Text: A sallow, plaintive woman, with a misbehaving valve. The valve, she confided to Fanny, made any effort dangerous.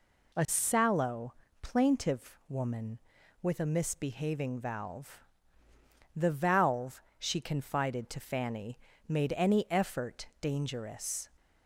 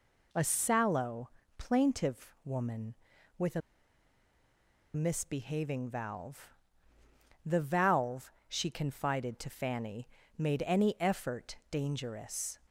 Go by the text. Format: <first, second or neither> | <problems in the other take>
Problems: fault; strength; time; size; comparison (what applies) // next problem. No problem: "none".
first | pauses between "a" and "misbehaving"; strong; at 3.6 s; 1.3 s long